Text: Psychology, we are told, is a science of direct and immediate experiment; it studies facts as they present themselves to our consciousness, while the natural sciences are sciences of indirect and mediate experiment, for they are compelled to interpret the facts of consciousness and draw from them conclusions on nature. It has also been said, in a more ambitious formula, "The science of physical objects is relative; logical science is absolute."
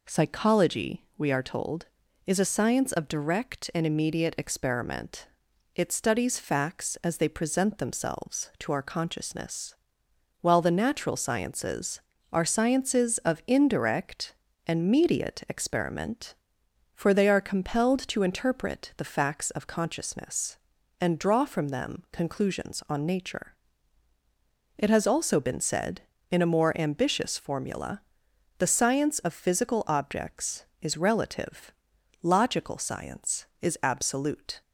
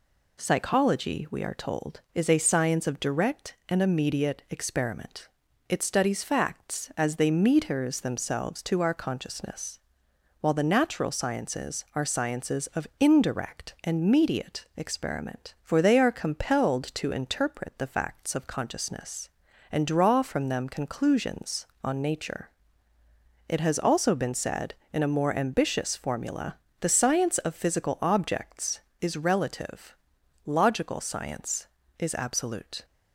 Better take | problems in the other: first | says "metres" for "present"; at 7.2 s

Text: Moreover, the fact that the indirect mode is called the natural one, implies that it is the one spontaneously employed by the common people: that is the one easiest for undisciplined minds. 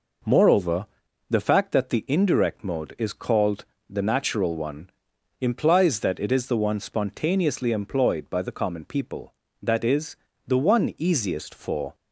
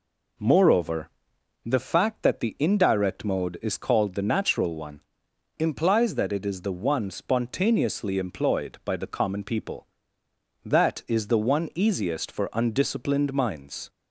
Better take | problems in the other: second | pauses between "called" and "the"; slight; at 3.6 s; 0.24 s long // pauses between "is" and "the"; slight; at 10.1 s; 0.32 s long // stops before "undisciplined minds"; at 11.9 s

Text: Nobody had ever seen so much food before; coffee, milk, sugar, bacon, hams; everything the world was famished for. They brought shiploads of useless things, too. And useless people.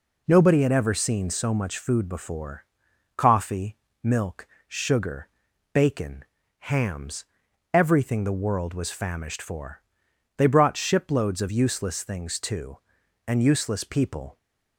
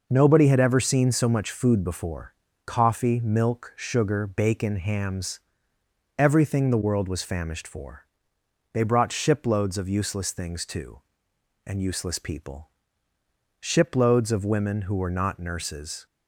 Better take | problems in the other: first | goes on to say "Shiploads of women who were not nurses"; strong; from 13.5 s on; 2.4 s long

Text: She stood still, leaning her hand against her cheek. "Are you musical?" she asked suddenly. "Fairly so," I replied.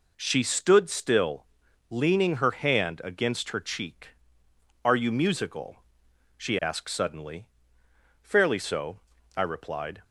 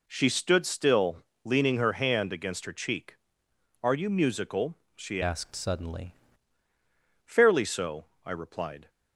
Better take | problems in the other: first | changes voice from "asked" to "suddenly"; from 5.2 to 6.1 s; 0.9 s long

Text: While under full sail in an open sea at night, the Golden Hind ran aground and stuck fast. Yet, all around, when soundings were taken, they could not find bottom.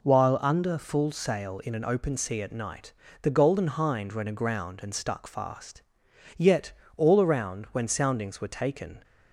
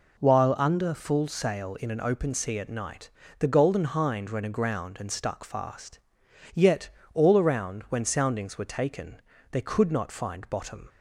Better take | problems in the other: second | stops before "they could not find bottom"; at 9.0 s

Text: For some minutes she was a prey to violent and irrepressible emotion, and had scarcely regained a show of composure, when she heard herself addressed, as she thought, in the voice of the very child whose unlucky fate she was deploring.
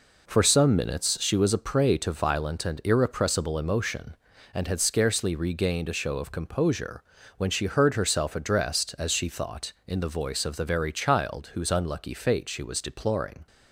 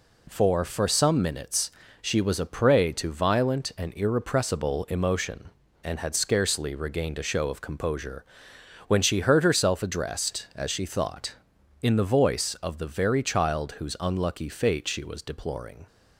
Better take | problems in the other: first | says "For" twice; at 0.6 s // pauses between "minutes" and "she"; slight; at 1.7 s; 0.32 s long

